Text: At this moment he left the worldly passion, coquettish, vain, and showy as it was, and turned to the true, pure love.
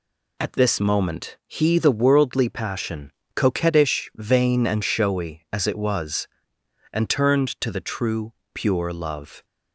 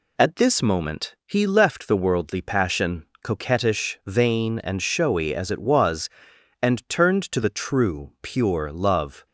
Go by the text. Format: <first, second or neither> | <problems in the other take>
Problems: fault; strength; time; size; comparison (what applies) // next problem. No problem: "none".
second | skips "left"; at 1.7 s